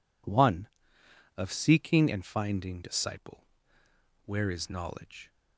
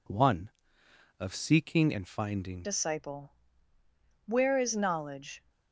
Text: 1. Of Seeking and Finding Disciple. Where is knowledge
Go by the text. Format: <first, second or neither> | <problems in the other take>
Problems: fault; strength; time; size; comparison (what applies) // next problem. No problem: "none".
first | changes voice at "Disciple"; from 2.6 s on; 2.8 s long